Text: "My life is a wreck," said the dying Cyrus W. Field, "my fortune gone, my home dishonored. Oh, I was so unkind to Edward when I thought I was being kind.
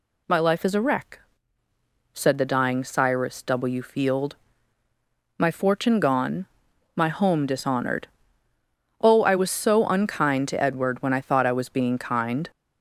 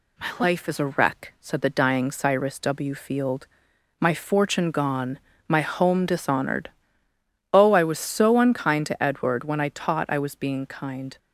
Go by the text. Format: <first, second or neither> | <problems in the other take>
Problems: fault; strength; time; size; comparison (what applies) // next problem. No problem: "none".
first | says "taught" for "thought"; at 9.7 s